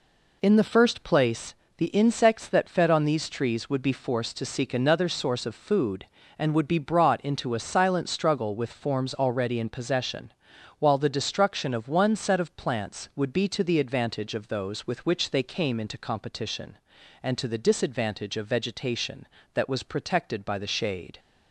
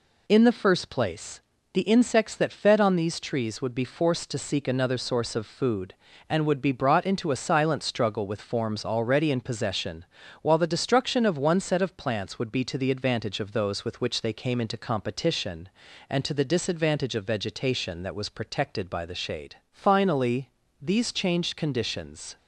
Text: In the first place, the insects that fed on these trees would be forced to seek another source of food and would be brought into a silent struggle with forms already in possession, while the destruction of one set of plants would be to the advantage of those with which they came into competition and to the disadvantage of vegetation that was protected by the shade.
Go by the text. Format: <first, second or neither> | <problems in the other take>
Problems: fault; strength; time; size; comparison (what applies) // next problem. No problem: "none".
first | goes on to say "Finally these changed conditions"; strong; from 19.7 s on; 2.6 s long